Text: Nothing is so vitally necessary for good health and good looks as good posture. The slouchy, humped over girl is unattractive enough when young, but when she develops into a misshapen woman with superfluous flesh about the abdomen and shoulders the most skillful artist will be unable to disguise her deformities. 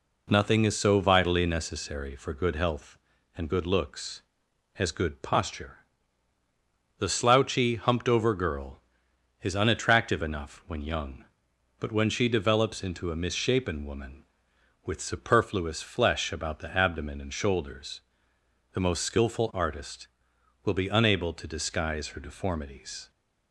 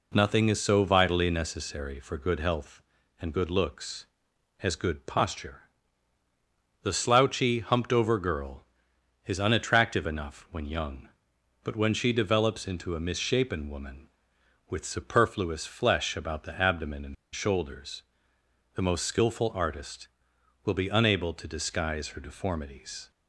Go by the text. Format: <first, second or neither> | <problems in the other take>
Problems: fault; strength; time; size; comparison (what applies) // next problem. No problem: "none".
first | pauses between "and" and "shoulders"; slight; at 17.1 s; 0.19 s long // pauses between "shoulders" and "the"; noticeable; at 18.0 s; 0.72 s long; noticeable in the first